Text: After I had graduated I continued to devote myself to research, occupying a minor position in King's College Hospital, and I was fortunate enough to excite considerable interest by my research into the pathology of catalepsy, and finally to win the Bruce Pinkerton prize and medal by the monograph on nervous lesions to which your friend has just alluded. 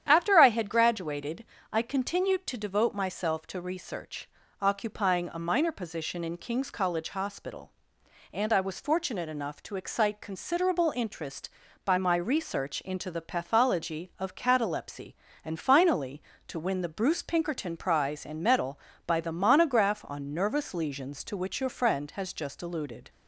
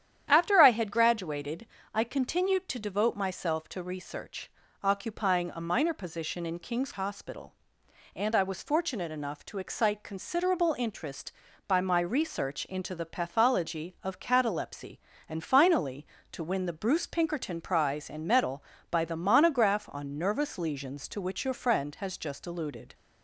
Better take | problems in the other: first | starts louder than the rest; strong; until 1.3 s; 10 dB; strong in the first // pauses between "graduated" and "I"; slight; at 1.6 s; 0.26 s long; slight in the first // skips "College"; at 6.9 s

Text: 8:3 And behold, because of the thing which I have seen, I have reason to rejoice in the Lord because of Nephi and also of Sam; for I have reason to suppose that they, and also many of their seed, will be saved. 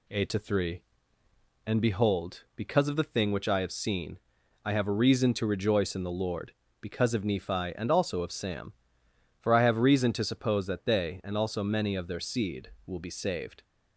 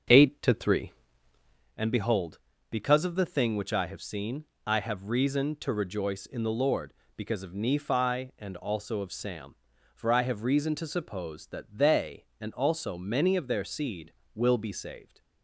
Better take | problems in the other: first | starts louder than the rest; until 1.7 s; 6.5 dB

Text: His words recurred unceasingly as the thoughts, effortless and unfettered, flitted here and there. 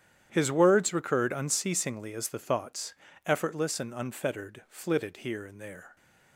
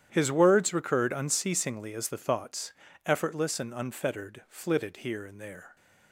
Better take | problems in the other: neither | starts louder than the rest; strong; the same in both

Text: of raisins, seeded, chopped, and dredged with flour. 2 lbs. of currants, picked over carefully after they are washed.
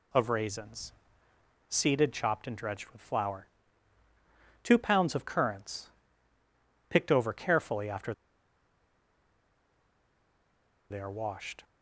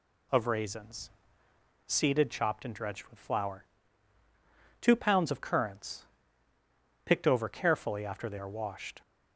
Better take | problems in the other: second | pauses between "after" and "they"; strong; at 8.1 s; 2.7 s long

